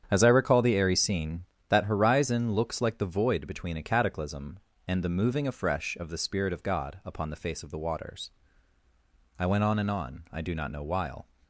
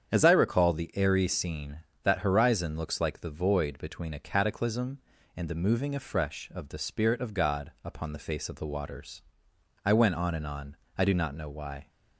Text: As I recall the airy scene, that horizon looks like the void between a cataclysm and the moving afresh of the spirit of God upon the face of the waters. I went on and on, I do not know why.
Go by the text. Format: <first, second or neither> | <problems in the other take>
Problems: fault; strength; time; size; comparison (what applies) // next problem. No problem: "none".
second | starts louder than the rest; strong; until 1.1 s; 8.5 dB; strong in the second // says "while" for "why"; at 10.8 s